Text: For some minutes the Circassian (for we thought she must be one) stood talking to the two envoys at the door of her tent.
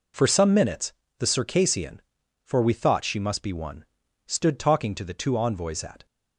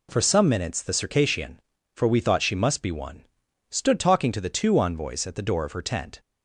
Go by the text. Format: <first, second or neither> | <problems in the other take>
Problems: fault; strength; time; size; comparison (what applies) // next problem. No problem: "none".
second | pauses between "minutes" and "the"; slight; at 0.9 s; 0.26 s long // stops before "the door of her tent"; at 6.0 s